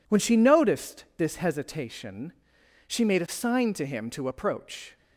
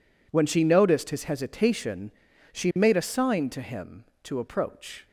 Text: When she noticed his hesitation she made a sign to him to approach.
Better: second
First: says "this" for "his"; at 1.1 s // pauses between "hesitation" and "she"; noticeable; at 2.3 s; 0.54 s long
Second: pauses between "hesitation" and "she"; at 2.1 s; 0.40 s long

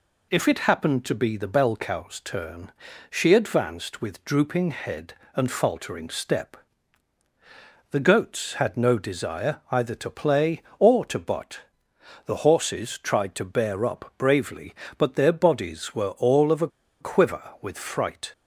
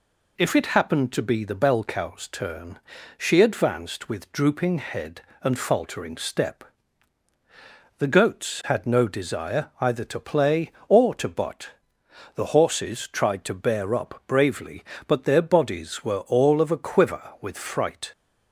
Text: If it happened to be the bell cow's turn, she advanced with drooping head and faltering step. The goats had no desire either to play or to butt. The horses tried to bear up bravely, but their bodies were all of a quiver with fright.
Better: second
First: pauses between "a" and "quiver"; slight; at 16.6 s; 0.32 s long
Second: none

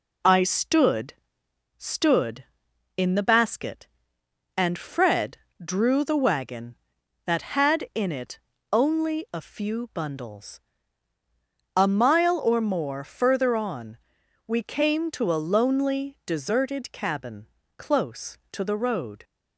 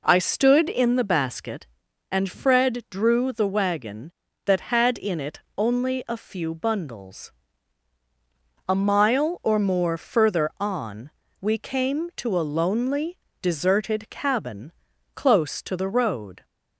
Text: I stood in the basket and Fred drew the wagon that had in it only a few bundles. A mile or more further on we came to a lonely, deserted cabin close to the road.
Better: second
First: says "stood" twice; at 1.7 s // pauses between "Fred" and "drew"; slight; at 5.3 s; 0.26 s long // pauses between "it" and "only"; slight; at 8.3 s; 0.30 s long // pauses between "on" and "we"; noticeable; at 13.9 s; 0.50 s long // pauses between "cabin" and "close"; slight; at 17.4 s; 0.32 s long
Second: pauses between "it" and "only"; slight; at 5.3 s; 0.16 s long // pauses between "on" and "we"; slight; at 11.0 s; 0.30 s long // pauses between "cabin" and "close"; at 14.7 s; 0.42 s long

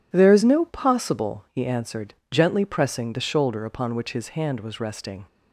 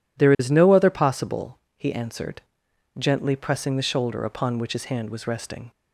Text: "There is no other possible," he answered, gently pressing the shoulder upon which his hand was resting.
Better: second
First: skips "other"; at 0.6 s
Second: none

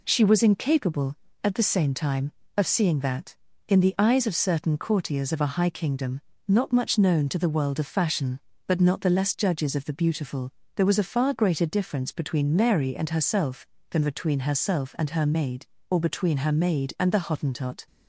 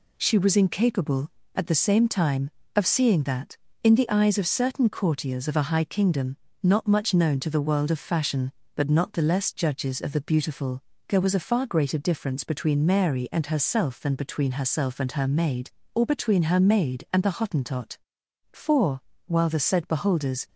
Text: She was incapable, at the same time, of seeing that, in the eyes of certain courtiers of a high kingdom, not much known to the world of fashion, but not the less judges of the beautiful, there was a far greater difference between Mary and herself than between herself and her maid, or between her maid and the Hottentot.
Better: first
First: none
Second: goes on to say "For while the said beholders"; strong; from 18.5 s on; 1.9 s long

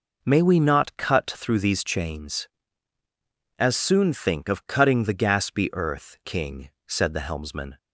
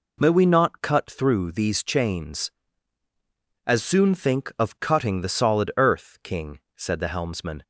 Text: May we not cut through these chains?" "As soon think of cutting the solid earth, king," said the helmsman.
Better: second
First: says "gaspy" for "solid"; at 5.1 s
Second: none

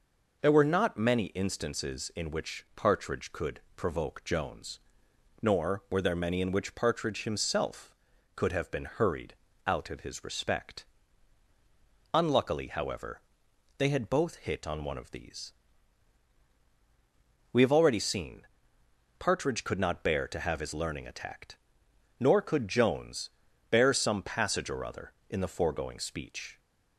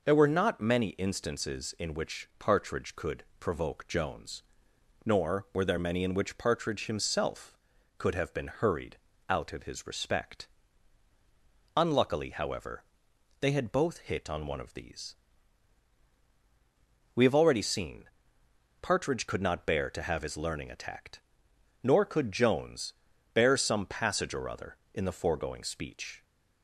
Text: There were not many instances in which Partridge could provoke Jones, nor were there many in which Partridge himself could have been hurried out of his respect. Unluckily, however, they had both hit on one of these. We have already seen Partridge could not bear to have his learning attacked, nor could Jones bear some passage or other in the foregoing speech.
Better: neither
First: pauses between "could" and "provoke"; slight; at 3.5 s; 0.16 s long // pauses between "hurried" and "out"; slight; at 9.3 s; 0.34 s long // pauses between "seen" and "Partridge"; noticeable; at 18.4 s; 0.72 s long // pauses between "Jones" and "bear"; at 23.3 s; 0.40 s long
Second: pauses between "could" and "provoke"; slight; at 3.2 s; 0.16 s long // pauses between "hurried" and "out"; slight; at 8.9 s; 0.34 s long // pauses between "seen" and "Partridge"; noticeable; at 18.0 s; 0.72 s long // pauses between "Jones" and "bear"; at 22.9 s; 0.40 s long

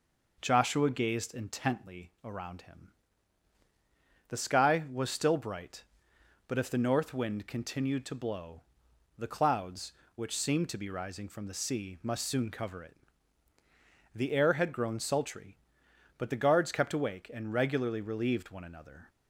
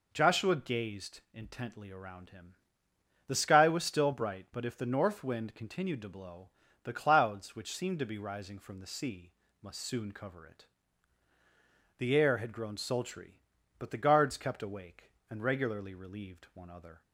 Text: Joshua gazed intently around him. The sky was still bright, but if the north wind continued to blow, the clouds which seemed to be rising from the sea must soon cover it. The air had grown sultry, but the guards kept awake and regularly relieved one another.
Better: first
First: none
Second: pauses between "sea" and "must"; slight; at 9.3 s; 0.30 s long // says "other" for "another"; at 16.7 s

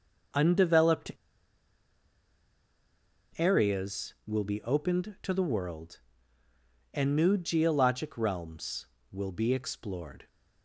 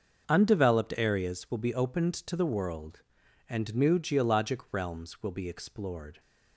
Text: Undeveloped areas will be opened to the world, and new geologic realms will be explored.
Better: second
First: starts louder than the rest; noticeable; until 3.5 s; 6 dB // pauses between "Undeveloped" and "areas"; strong; at 1.1 s; 2.2 s long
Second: starts louder than the rest; until 1.2 s; 6 dB

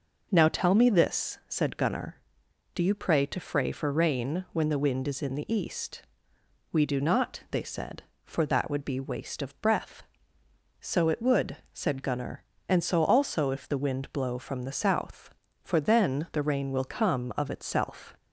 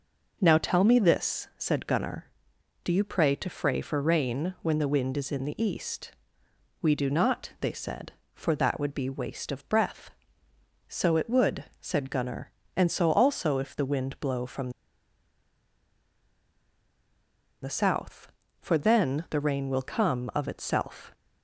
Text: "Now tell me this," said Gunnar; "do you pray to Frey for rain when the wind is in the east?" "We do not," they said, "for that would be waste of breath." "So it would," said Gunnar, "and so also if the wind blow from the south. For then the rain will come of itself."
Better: first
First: none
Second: pauses between "from" and "the"; strong; at 14.7 s; 2.9 s long

